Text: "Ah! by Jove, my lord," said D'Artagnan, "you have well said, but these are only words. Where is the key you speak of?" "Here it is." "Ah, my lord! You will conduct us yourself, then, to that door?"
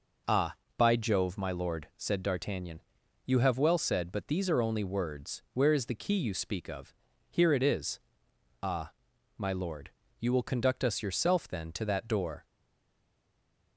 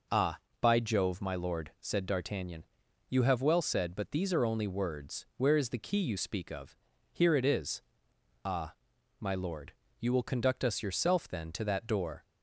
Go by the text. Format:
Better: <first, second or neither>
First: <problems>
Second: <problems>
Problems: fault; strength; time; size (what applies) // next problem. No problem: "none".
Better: second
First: stays silent after the last word; noticeable; from 12.4 s on; 1.3 s long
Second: none